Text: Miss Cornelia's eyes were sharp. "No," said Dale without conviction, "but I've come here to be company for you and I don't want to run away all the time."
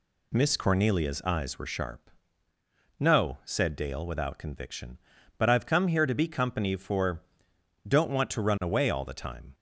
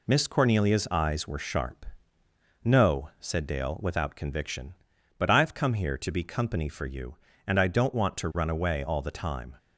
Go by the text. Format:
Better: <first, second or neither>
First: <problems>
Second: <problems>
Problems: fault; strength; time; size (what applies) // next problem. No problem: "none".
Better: second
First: skips "you and I"; at 7.5 s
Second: none